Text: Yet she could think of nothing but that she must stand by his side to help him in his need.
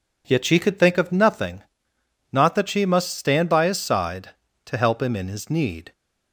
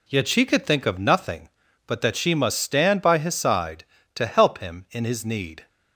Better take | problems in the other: second | says "not" for "but"; at 2.3 s

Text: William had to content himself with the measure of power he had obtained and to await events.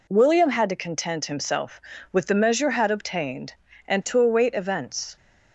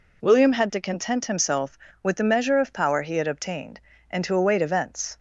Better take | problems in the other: second | skips "of power he"; at 2.6 s

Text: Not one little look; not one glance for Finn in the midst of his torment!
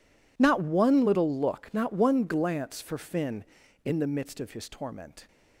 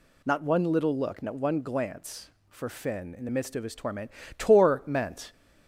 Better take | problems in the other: first | says "torment" twice; at 4.3 s

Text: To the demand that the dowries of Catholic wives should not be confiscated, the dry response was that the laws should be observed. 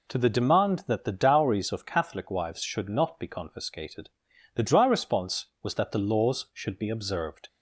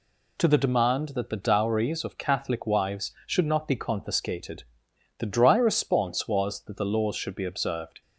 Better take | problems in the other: neither | none

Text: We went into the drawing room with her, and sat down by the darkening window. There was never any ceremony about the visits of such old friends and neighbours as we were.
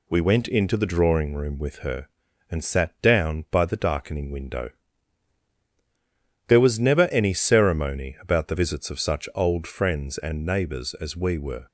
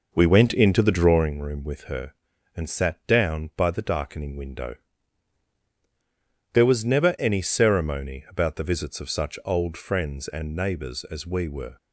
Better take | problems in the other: first | starts louder than the rest; noticeable; until 1.3 s; 5 dB

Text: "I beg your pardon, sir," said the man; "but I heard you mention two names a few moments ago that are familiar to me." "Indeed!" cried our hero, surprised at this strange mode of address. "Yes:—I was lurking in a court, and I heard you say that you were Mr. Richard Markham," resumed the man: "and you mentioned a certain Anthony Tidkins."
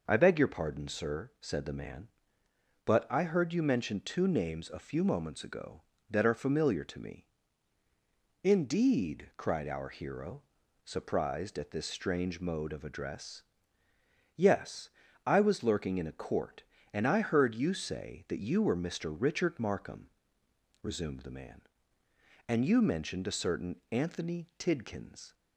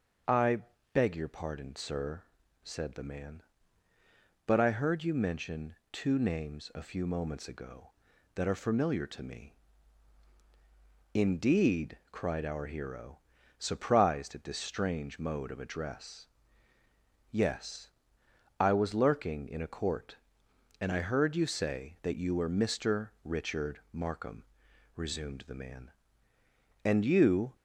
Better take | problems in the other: first | starts louder than the rest; until 1.6 s; 6.5 dB // pauses between "I" and "beg"; slight; at 0.5 s; 0.34 s long // pauses between "mention" and "two"; slight; at 5.7 s; 0.16 s long // stops before "mentioned a certain Anthony Tidkins"; at 27.5 s

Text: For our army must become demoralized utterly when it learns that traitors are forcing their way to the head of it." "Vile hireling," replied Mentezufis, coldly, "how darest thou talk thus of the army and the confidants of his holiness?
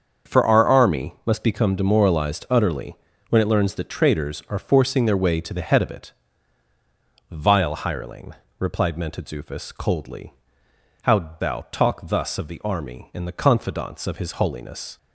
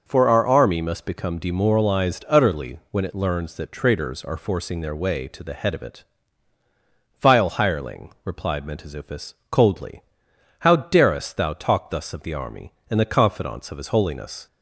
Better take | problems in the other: second | starts louder than the rest; until 1.3 s; 7 dB // pauses between "utterly" and "when"; slight; at 2.9 s; 0.32 s long // skips "darest"; at 11.3 s

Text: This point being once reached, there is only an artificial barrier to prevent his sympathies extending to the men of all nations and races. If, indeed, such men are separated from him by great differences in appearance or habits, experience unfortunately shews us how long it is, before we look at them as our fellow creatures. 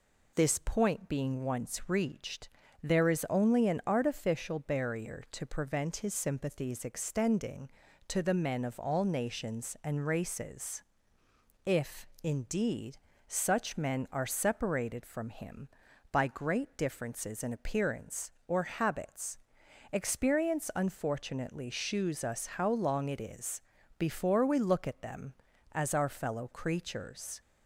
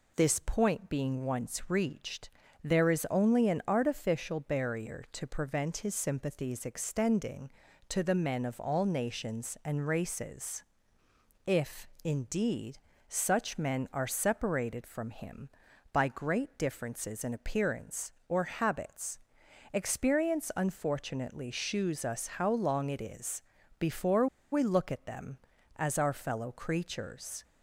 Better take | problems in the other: first | pauses between "before" and "we"; slight; at 24.2 s; 0.26 s long

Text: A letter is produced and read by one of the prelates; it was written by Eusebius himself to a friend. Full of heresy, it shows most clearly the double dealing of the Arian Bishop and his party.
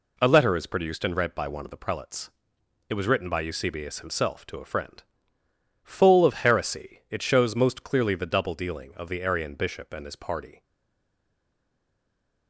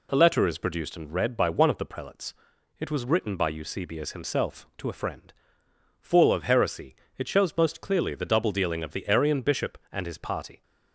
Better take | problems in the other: second | stays silent after the last word; noticeable; from 10.6 s on; 1.8 s long

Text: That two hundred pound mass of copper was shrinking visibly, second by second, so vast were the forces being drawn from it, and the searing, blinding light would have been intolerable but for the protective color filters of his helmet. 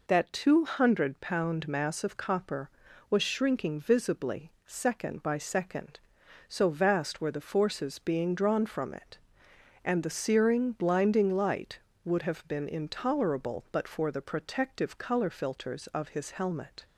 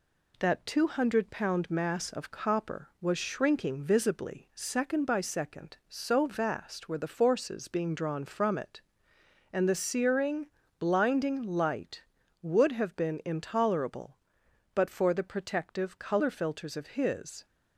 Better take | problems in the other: first | stops before "helmet"; at 17.4 s

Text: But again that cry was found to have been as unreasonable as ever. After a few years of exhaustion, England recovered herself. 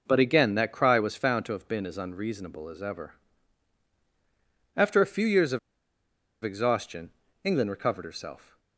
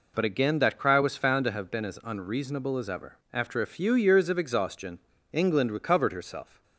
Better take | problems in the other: second | pauses between "of" and "exhaustion"; noticeable; at 5.5 s; 0.85 s long

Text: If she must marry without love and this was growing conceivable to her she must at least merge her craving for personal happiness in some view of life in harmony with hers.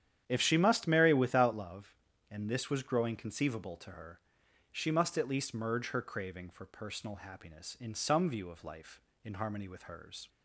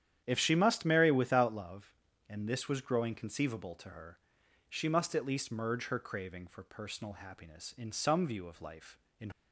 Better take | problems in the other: first | starts louder than the rest; strong; until 1.2 s; 9.5 dB; strong in the first // pauses between "her" and "she"; noticeable; at 4.1 s; 0.50 s long; noticeable in the first // stops before "harmony with hers"; at 9.3 s

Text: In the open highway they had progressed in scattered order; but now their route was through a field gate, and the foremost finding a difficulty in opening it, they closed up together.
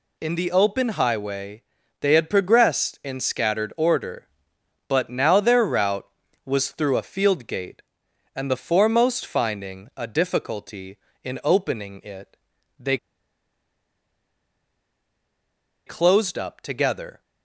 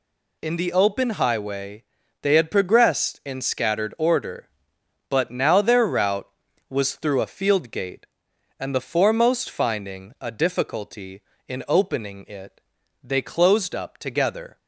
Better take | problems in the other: second | pauses between "highway" and "they"; at 1.6 s; 0.38 s long; also in the second // pauses between "they" and "closed"; strong; at 12.9 s; 2.8 s long

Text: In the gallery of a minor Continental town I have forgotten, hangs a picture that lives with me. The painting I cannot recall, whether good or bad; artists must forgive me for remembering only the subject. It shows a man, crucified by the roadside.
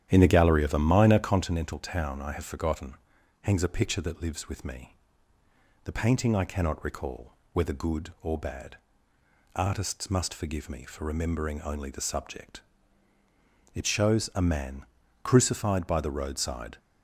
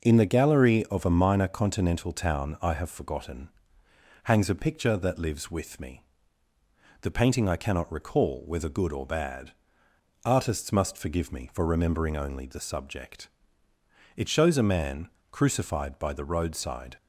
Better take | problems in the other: second | starts louder than the rest; strong; until 1.4 s; 10.5 dB

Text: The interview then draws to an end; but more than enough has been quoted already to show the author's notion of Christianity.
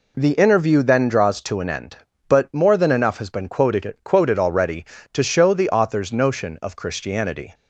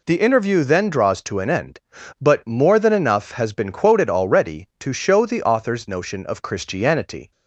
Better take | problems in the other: second | says "quoted" twice; at 4.0 s

